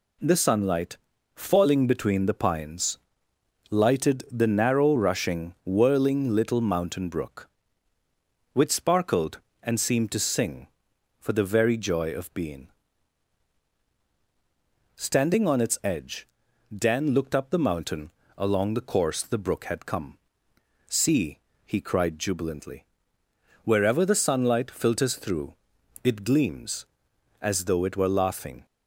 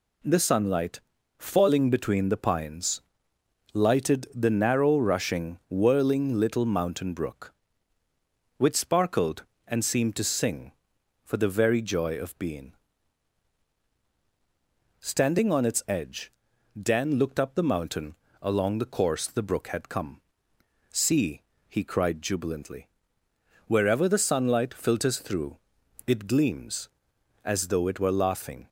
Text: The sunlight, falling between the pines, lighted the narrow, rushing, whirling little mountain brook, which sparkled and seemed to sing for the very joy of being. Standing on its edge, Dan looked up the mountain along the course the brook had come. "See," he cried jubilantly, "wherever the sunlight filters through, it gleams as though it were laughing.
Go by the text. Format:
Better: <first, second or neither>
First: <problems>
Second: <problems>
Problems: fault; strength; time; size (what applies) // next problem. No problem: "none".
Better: neither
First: pauses between "mountain" and "along"; slight; at 18.0 s; 0.28 s long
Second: pauses between "mountain" and "along"; slight; at 18.1 s; 0.28 s long